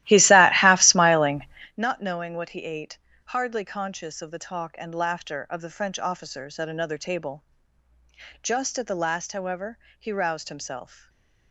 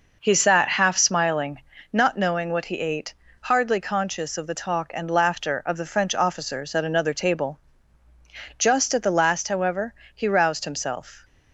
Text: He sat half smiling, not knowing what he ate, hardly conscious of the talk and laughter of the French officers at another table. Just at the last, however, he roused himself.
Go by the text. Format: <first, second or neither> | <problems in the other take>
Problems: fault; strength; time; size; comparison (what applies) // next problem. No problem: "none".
second | starts louder than the rest; strong; until 1.8 s; 15.5 dB // stays silent after the last word; slight; from 10.9 s on; 0.6 s long